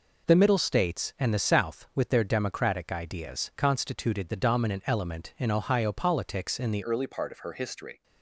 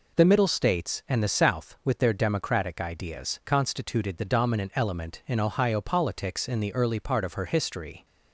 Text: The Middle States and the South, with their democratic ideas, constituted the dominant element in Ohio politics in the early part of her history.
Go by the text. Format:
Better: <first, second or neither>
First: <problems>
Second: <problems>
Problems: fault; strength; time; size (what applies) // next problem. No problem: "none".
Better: second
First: changes voice at "early"; from 6.8 s on; 1.2 s long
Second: none